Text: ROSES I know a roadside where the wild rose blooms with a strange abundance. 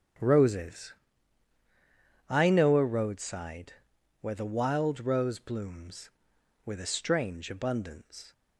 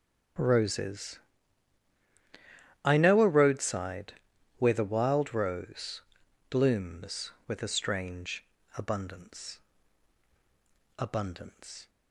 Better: first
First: starts louder than the rest; strong; until 2.5 s; 7.5 dB // pauses between "ROSES" and "I"; strong; at 0.9 s; 1.3 s long // pauses between "roadside" and "where"; noticeable; at 3.7 s; 0.49 s long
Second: starts louder than the rest; strong; until 3.0 s; 8 dB // pauses between "ROSES" and "I"; strong; at 1.1 s; 1.6 s long // pauses between "roadside" and "where"; noticeable; at 4.1 s; 0.46 s long // pauses between "rose" and "blooms"; noticeable; at 6.0 s; 0.48 s long // pauses between "strange" and "abundance"; slight; at 8.4 s; 0.32 s long // says "abundance" twice; at 10.9 s

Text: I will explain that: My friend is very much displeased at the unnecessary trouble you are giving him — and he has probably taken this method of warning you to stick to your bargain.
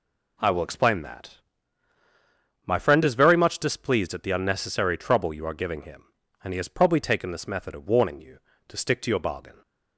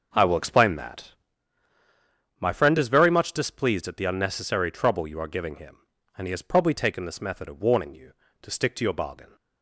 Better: first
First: none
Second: starts louder than the rest; noticeable; until 1.4 s; 6 dB

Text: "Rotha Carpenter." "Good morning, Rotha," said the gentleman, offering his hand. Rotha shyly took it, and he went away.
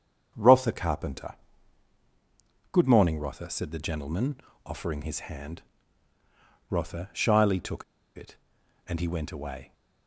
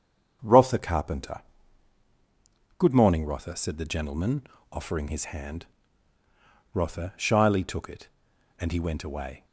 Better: second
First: starts louder than the rest; strong; until 1.3 s; 7 dB // pauses between "took" and "it"; slight; at 7.8 s; 0.33 s long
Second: starts louder than the rest; strong; until 1.4 s; 7 dB

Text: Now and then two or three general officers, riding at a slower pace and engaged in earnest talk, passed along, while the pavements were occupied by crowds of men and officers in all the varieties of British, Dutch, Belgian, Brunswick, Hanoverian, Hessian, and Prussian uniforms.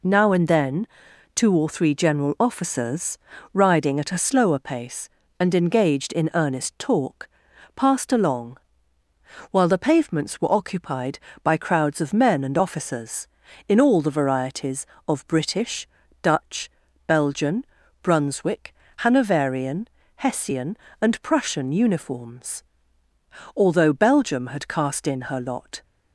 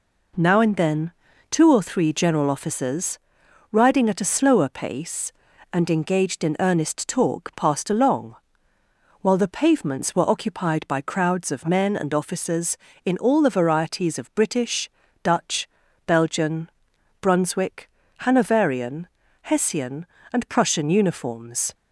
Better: second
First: pauses between "then" and "two"; noticeable; at 0.8 s; 0.48 s long // goes on to say "Although Belgium had cast in her lot"; strong; from 23.5 s on; 2.2 s long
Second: pauses between "then" and "two"; at 1.1 s; 0.38 s long

